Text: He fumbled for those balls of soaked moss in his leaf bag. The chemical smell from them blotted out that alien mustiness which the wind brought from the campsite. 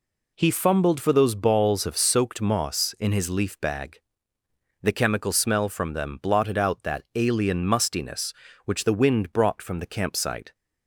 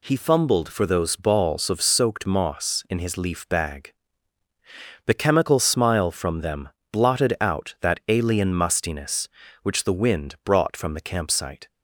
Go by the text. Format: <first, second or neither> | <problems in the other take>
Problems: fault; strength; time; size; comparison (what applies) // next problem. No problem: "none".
first | says "smile" for "smell"; at 5.6 s // pauses between "them" and "blotted"; slight; at 6.7 s; 0.22 s long